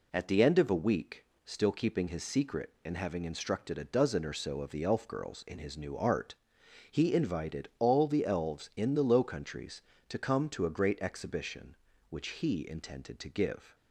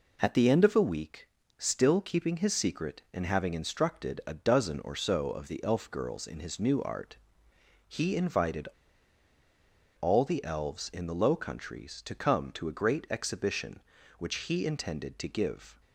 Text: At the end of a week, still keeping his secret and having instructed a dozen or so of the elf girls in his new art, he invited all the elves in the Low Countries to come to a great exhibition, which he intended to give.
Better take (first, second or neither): first